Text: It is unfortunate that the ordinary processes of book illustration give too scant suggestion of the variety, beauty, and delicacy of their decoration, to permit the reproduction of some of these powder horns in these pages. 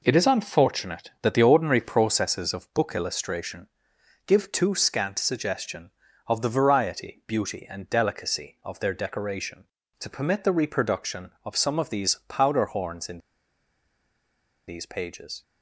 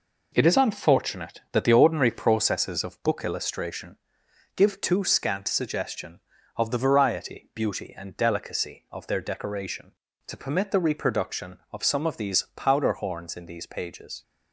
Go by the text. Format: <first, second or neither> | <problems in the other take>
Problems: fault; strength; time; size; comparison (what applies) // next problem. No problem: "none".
second | pauses between "illustration" and "give"; noticeable; at 3.6 s; 0.60 s long; noticeable in the second // pauses between "in" and "these"; strong; at 13.1 s; 1.4 s long